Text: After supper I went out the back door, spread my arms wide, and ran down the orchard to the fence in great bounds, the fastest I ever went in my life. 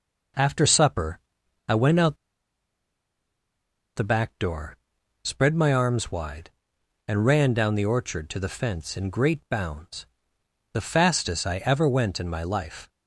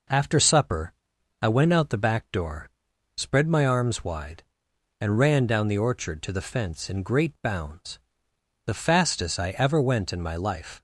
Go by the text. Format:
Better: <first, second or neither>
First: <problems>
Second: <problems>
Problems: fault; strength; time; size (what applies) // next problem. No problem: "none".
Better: second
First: pauses between "supper" and "I"; noticeable; at 1.1 s; 0.50 s long // pauses between "out" and "the"; strong; at 2.1 s; 1.7 s long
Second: pauses between "supper" and "I"; noticeable; at 0.9 s; 0.50 s long